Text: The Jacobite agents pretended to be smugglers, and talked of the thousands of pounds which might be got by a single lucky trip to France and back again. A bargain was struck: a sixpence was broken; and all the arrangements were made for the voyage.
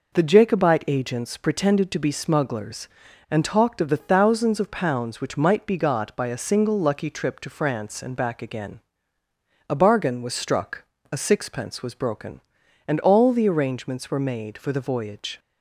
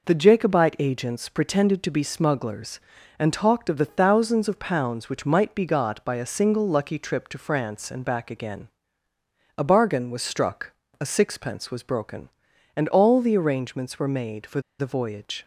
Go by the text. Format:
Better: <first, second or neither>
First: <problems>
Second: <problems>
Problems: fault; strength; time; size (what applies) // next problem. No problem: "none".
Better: first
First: none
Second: pauses between "for" and "the"; slight; at 14.6 s; 0.18 s long